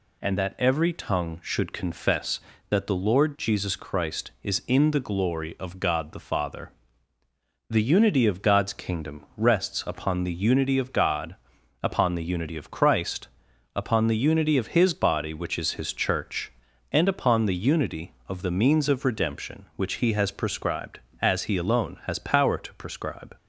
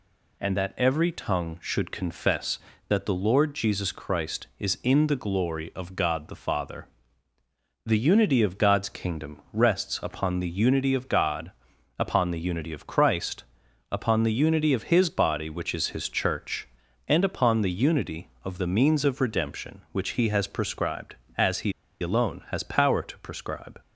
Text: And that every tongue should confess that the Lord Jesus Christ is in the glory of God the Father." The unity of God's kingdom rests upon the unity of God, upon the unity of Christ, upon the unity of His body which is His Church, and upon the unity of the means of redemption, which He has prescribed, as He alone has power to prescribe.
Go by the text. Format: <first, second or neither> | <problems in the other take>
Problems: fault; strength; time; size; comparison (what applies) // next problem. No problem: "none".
first | pauses between "He" and "alone"; slight; at 21.7 s; 0.28 s long